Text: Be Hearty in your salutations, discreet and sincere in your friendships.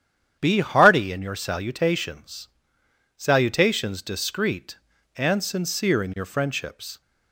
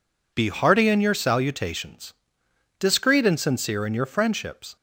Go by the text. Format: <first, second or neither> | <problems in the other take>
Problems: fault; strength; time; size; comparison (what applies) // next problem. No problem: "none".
second | starts louder than the rest; strong; until 1.4 s; 9 dB // says "salutations" twice; at 3.1 s